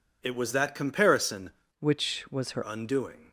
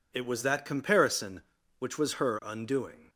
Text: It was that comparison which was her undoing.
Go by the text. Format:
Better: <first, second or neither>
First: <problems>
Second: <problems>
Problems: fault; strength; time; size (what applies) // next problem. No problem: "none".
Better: second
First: changes voice from "which" to "her"; from 1.7 to 2.6 s; 0.9 s long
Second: none